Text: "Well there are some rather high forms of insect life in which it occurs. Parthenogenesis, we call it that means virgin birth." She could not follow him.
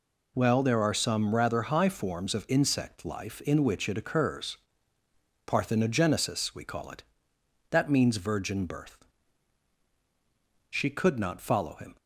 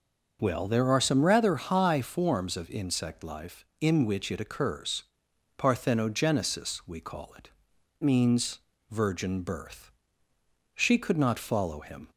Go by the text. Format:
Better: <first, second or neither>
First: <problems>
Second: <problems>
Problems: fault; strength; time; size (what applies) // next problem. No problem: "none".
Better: first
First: none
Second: skips "that"; at 7.7 s // pauses between "means" and "virgin"; slight; at 8.5 s; 0.32 s long